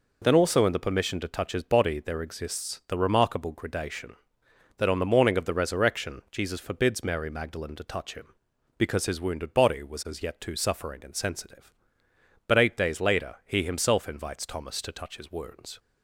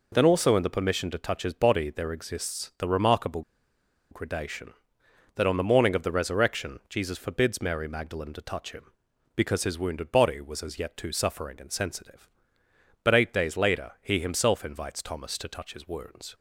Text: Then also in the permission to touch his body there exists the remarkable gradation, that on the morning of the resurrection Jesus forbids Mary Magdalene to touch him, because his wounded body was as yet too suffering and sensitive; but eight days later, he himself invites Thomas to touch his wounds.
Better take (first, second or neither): first